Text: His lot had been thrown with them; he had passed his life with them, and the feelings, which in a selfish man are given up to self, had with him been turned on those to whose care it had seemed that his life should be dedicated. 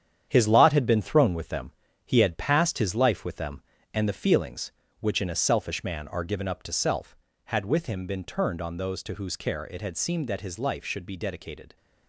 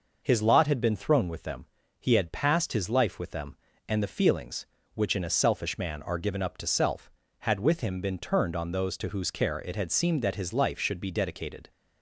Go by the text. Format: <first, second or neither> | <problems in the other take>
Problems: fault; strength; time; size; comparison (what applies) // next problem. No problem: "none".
second | gets quieter; strong; throughout; 7.5 dB